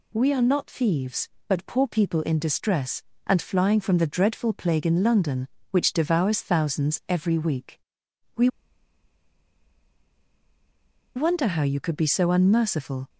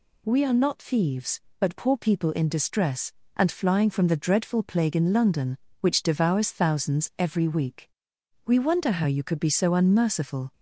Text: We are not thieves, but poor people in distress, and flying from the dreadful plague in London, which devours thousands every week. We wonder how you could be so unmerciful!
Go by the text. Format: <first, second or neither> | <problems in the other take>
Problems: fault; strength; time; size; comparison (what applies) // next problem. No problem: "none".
second | pauses between "We" and "wonder"; strong; at 8.4 s; 2.6 s long